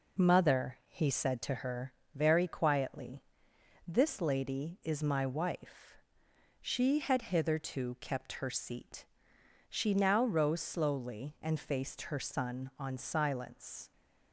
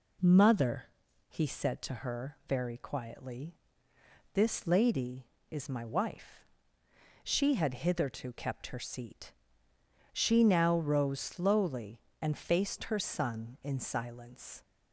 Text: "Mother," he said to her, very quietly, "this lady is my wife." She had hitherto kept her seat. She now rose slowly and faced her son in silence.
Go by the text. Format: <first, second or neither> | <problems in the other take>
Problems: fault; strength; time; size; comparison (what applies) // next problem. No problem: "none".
second | says "on" for "in"; at 12.7 s